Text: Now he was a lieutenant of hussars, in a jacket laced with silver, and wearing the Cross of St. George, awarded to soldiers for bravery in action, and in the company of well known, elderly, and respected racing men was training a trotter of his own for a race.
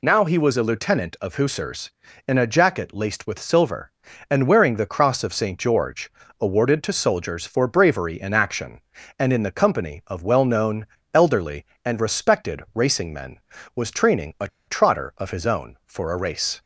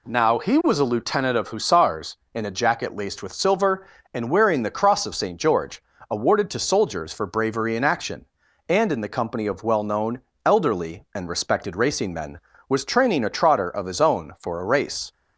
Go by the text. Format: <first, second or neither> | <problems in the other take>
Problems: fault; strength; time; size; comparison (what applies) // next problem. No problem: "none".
second | pauses between "a" and "trotter"; slight; at 14.4 s; 0.20 s long